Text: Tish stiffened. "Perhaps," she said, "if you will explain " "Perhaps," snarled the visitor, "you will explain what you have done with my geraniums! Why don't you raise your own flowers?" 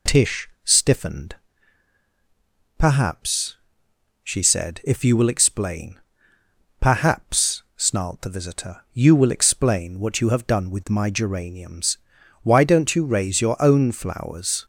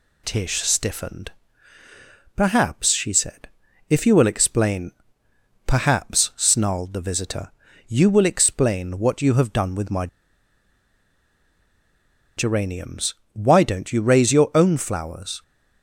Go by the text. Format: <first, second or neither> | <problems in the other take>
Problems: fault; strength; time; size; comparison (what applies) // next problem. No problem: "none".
first | pauses between "my" and "geraniums"; strong; at 10.0 s; 2.3 s long